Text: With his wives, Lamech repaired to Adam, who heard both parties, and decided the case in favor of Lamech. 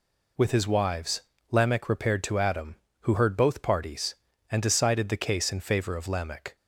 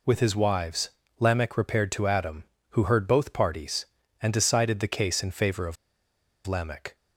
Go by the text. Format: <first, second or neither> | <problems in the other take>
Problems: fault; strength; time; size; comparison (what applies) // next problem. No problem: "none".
first | pauses between "of" and "Lamech"; noticeable; at 5.7 s; 0.71 s long